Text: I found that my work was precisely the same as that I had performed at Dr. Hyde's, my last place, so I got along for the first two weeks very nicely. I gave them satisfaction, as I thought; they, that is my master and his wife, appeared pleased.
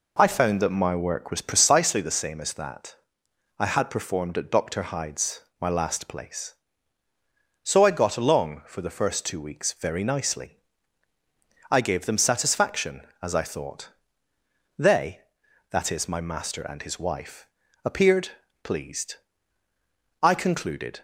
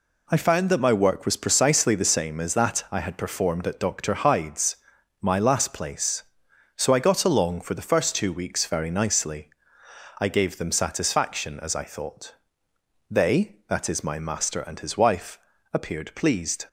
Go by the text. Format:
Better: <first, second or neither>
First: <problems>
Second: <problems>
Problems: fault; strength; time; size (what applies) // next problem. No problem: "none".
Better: second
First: pauses between "that" and "I"; noticeable; at 2.9 s; 0.64 s long // pauses between "appeared" and "pleased"; slight; at 18.2 s; 0.34 s long // goes on to say "I concluded"; noticeable; from 20.2 s on; 0.78 s long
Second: none